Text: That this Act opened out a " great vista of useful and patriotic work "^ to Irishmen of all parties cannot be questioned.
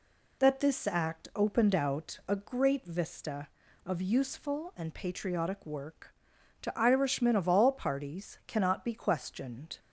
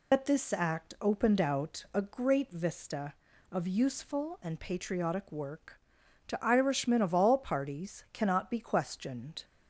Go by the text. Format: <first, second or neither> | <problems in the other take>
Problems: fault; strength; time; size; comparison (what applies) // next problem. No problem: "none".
first | loses the start of "That"; at 0.1 s; 55 ms